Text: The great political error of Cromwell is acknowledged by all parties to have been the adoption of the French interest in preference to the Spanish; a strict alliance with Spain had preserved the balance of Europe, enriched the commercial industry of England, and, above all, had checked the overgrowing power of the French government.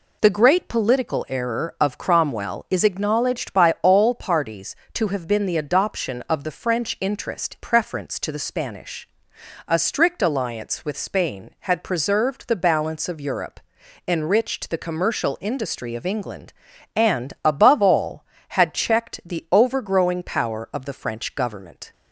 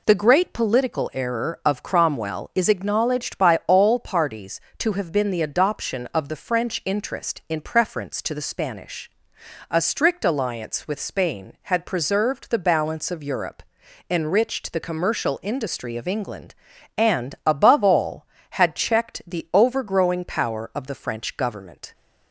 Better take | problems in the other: second | skips "in"; at 7.5 s

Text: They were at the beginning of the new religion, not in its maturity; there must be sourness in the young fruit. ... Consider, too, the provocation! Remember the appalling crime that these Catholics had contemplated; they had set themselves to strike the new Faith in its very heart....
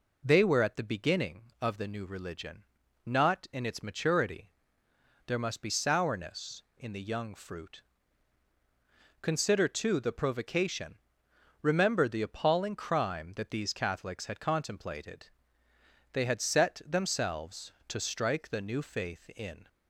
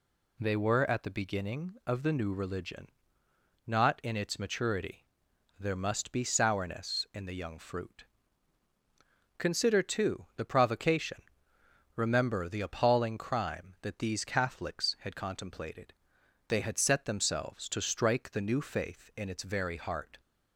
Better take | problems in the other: second | stops before "its very heart"; at 19.6 s

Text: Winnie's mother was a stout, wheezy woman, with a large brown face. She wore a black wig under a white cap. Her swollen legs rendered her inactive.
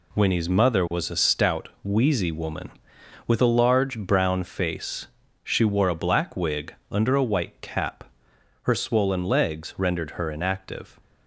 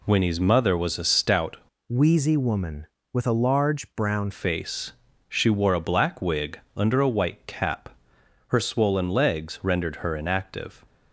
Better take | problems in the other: first | changes voice from "wheezy" to "brown"; from 1.8 to 4.3 s; 2.5 s long // pauses between "wig" and "under"; slight; at 6.5 s; 0.16 s long; slight in the first

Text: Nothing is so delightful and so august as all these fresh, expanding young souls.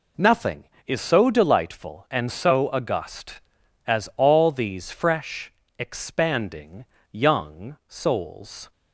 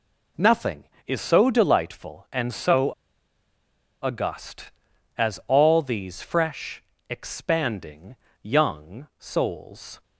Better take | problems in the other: first | pauses between "so" and "august"; at 2.9 s; 1.1 s long // pauses between "expanding" and "young"; slight; at 8.1 s; 0.28 s long; slight in the first

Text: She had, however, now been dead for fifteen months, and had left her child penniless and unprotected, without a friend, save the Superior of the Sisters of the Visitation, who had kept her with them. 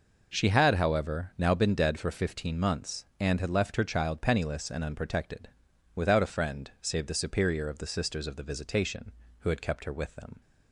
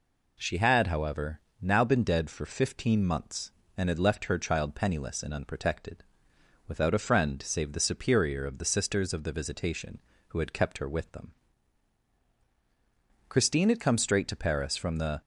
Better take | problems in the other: first | goes on to say "Christine had come straight to Paris from the"; strong; from 13.2 s on; 1.9 s long

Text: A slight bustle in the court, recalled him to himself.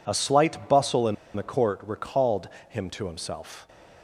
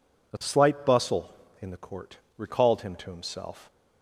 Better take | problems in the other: second | pauses between "in" and "the"; slight; at 1.1 s; 0.20 s long // pauses between "recalled" and "him"; slight; at 2.4 s; 0.20 s long

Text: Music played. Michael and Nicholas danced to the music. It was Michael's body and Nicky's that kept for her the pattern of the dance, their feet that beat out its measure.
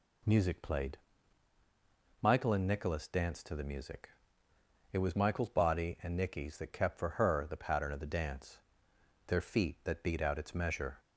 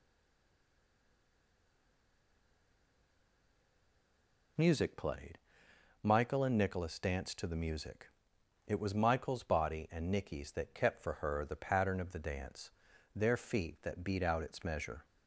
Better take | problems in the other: first | stays silent before the first word; strong; until 4.5 s; 4.5 s long

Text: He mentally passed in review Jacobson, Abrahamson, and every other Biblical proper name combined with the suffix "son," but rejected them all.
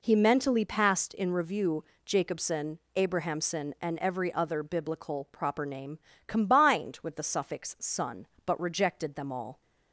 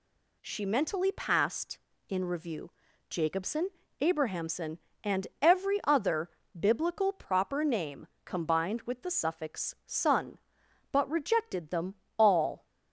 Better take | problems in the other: first | says "She" for "He"; at 0.4 s // pauses between "review" and "Jacobson"; at 2.7 s; 0.38 s long; slight in the first // pauses between "other" and "Biblical"; slight; at 6.2 s; 0.30 s long // pauses between "name" and "combined"; slight; at 8.0 s; 0.18 s long; slight in the first // pauses between "them" and "all"; slight; at 11.9 s; 0.24 s long

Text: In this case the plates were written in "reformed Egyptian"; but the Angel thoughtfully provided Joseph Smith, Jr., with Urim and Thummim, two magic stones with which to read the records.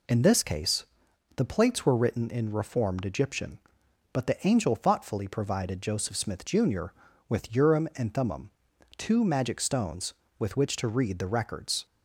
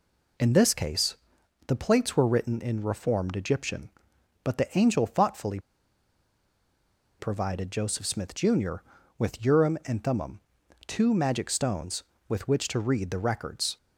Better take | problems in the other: first | pauses between "case" and "the"; noticeable; at 1.1 s; 0.52 s long; noticeable in the first // pauses between "thoughtfully" and "provided"; strong; at 5.5 s; 1.6 s long

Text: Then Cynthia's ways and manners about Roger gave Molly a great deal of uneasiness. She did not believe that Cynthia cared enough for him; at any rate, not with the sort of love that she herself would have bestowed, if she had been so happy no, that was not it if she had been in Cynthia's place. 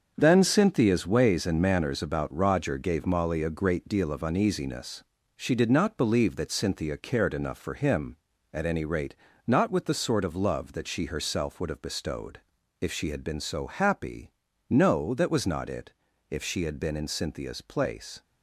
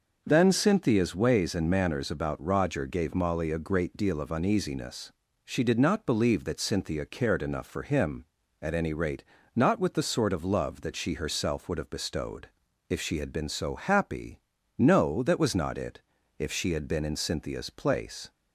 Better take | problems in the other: second | gets quieter; strong; throughout; 8.5 dB // pauses between "happy" and "no"; at 14.3 s; 0.40 s long; also in the second // pauses between "it" and "if"; at 15.9 s; 0.38 s long; also in the second

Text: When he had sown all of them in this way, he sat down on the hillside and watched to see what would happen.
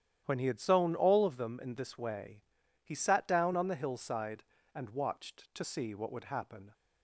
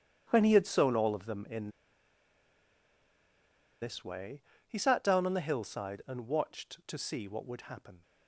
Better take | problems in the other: first | starts louder than the rest; strong; until 1.2 s; 10 dB; strong in the first // pauses between "in" and "this"; strong; at 1.6 s; 2.1 s long

